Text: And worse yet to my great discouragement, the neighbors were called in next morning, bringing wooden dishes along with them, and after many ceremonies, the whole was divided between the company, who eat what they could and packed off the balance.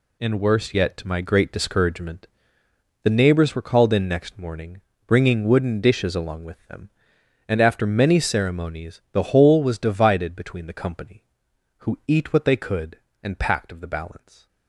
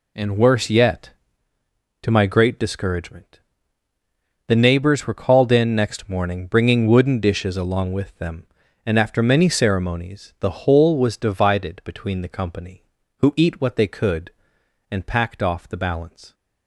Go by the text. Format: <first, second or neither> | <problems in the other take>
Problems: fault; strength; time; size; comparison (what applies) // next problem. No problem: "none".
second | says "of" for "off"; at 13.7 s // stays silent after the last word; slight; from 14.1 s on; 0.5 s long